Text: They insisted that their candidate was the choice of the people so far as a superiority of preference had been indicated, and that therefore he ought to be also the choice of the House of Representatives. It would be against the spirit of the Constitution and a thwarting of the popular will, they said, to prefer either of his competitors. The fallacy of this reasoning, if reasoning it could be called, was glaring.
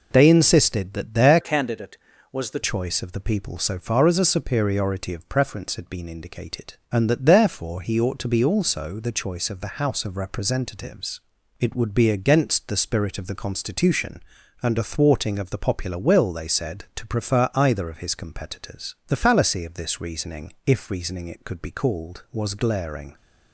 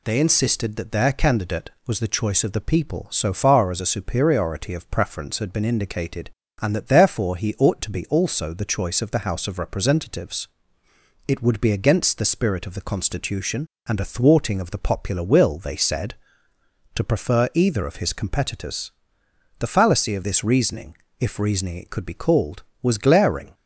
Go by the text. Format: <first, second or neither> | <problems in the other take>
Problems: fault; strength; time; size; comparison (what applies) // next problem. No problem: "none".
second | changes voice from "candidate" to "the"; from 1.4 to 2.5 s; 1.1 s long